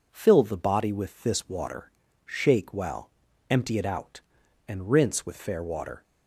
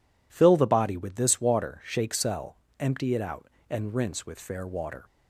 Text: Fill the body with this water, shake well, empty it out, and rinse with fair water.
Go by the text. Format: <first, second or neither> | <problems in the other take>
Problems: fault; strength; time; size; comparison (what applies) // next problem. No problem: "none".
first | says "cell" for "well"; at 2.1 s